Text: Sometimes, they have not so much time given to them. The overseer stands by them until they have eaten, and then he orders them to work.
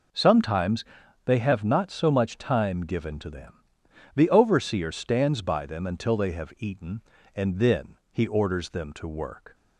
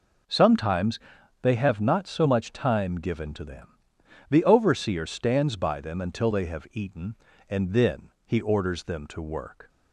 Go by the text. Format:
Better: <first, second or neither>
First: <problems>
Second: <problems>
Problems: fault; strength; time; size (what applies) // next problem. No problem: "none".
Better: neither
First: pauses between "then" and "he"; slight; at 7.9 s; 0.16 s long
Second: pauses between "then" and "he"; slight; at 8.1 s; 0.16 s long